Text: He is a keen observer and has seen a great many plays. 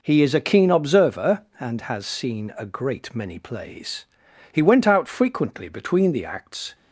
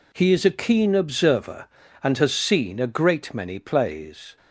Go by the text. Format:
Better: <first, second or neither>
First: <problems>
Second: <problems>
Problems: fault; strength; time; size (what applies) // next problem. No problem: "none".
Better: second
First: goes on to say "He went out frequently between the acts"; strong; from 4.5 s on; 2.2 s long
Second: none